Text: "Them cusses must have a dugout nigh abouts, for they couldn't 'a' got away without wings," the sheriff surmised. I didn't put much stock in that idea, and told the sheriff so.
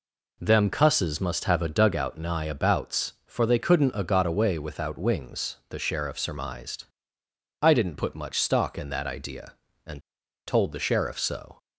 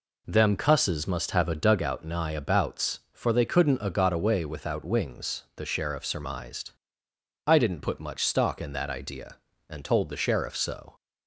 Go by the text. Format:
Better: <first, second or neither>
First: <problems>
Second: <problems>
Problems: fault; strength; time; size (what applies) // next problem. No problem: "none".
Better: second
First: pauses between "and" and "told"; noticeable; at 10.0 s; 0.46 s long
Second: none